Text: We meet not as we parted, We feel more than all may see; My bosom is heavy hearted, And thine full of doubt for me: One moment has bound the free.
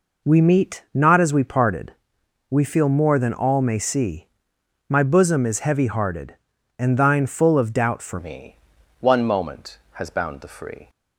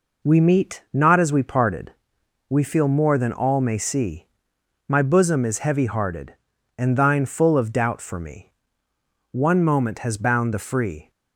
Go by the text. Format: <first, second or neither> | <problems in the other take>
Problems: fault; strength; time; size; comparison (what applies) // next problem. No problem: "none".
second | changes voice at "me"; from 8.1 s on; 2.7 s long